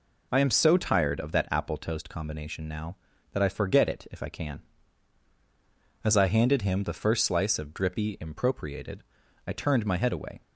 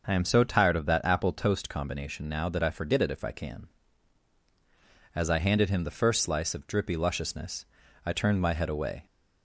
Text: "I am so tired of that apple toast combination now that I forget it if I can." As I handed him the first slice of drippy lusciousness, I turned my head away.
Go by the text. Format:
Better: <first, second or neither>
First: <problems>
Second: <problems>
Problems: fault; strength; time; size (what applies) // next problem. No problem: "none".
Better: second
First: says "impropriated" for "lusciousness"; at 8.1 s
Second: none